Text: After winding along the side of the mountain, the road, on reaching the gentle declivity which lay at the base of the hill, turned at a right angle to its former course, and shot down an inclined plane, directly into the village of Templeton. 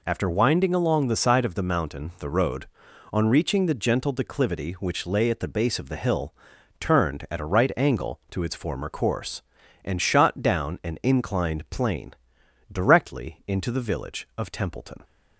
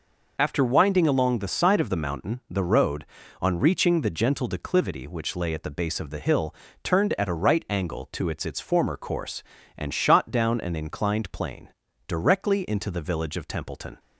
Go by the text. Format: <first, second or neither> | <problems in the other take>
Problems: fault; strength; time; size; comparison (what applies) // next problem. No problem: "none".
first | says "its" twice; at 8.4 s